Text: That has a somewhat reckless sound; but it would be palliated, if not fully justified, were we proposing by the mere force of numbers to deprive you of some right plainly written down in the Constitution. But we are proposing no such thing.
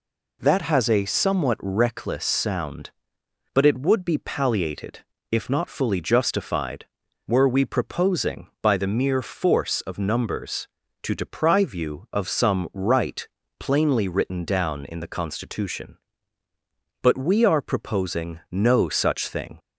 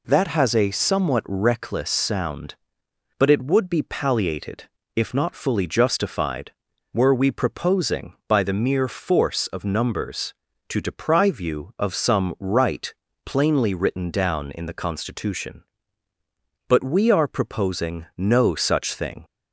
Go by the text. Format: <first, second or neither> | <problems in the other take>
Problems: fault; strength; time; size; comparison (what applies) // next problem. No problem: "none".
neither | pauses between "right" and "plainly"; slight; the same in both